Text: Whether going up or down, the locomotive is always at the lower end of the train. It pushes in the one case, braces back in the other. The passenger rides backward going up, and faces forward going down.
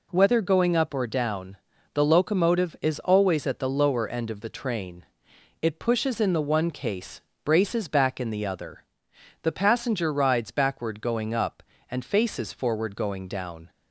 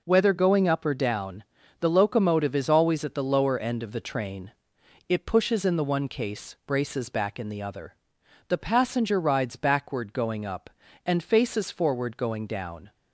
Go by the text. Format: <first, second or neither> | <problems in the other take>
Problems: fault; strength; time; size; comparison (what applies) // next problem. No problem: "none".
neither | none